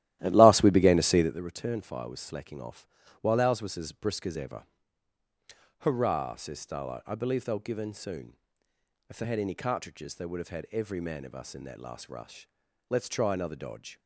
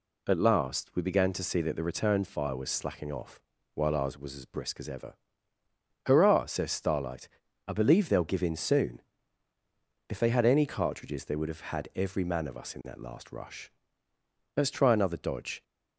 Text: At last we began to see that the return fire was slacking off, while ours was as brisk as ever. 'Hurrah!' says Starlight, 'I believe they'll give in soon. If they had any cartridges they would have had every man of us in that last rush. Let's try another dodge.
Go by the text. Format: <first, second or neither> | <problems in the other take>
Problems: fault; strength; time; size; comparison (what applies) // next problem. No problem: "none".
second | starts louder than the rest; strong; until 1.4 s; 14 dB